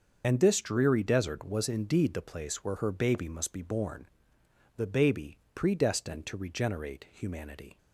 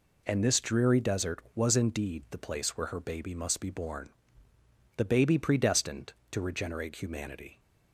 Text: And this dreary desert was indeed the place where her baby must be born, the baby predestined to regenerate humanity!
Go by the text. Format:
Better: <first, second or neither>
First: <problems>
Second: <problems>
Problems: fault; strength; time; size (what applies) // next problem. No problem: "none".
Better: second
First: loses the start of "And"; at 0.2 s; 35 ms // starts louder than the rest; until 1.2 s; 6.5 dB // pauses between "baby" and "predestined"; slight; at 5.3 s; 0.18 s long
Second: none